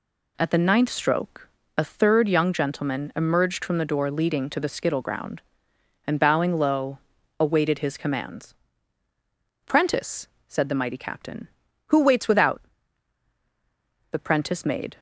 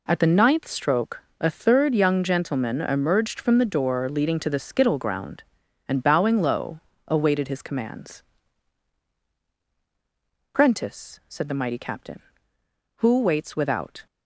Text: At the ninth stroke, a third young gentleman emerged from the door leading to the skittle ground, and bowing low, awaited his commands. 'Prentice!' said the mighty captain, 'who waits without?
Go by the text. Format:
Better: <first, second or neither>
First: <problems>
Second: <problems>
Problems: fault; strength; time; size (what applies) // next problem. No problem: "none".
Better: second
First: goes on to say "The prentice made"; noticeable; from 14.1 s on; 0.86 s long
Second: none